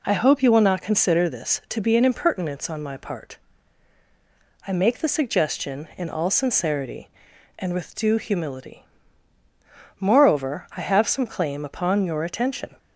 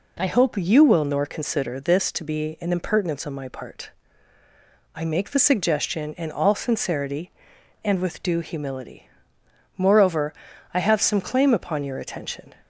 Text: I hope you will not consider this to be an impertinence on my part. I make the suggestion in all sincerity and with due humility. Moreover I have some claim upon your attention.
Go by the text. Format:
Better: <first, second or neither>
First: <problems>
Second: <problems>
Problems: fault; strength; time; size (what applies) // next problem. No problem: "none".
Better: first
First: none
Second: says "nor" for "not"; at 1.0 s // pauses between "Moreover" and "I"; at 10.3 s; 0.40 s long